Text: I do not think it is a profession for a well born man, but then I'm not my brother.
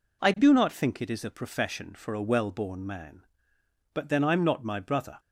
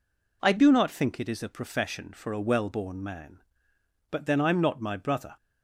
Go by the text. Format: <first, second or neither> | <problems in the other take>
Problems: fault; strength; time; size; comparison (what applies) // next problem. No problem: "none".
neither | none